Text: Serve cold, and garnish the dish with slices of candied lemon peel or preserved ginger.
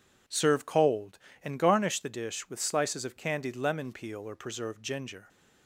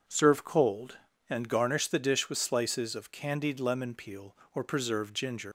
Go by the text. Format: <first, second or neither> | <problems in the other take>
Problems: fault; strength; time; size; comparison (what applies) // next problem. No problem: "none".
first | leaves "ginger" unfinished; at 5.4 s; 145 ms